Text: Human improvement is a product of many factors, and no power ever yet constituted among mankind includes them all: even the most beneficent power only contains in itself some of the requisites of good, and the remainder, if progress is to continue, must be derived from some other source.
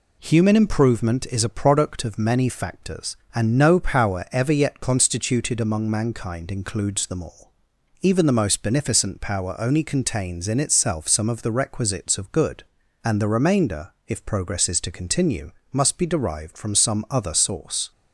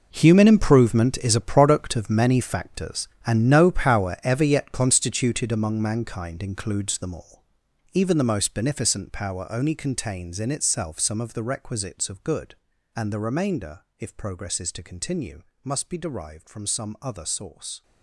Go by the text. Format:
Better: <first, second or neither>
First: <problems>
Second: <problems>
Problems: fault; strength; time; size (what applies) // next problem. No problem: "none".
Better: first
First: none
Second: gets quieter; strong; throughout; 15 dB